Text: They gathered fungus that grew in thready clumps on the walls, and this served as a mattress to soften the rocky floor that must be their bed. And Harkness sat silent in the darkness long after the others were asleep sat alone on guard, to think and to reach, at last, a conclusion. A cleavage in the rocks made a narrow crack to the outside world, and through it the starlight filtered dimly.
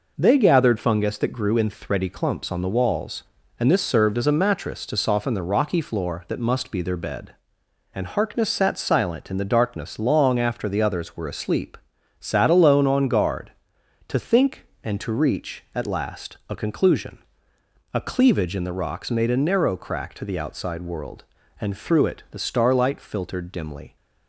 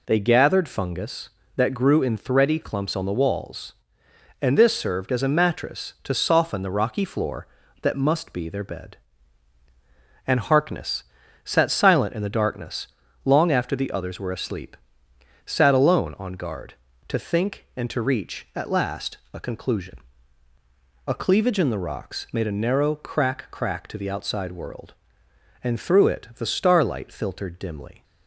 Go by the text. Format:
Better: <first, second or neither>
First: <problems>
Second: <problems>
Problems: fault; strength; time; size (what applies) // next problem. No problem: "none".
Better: first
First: pauses between "asleep" and "sat"; at 11.7 s; 0.40 s long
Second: pauses between "Harkness" and "sat"; at 11.0 s; 0.42 s long // pauses between "darkness" and "long"; at 12.8 s; 0.38 s long // pauses between "asleep" and "sat"; noticeable; at 14.7 s; 0.66 s long // says "crack" twice; at 23.5 s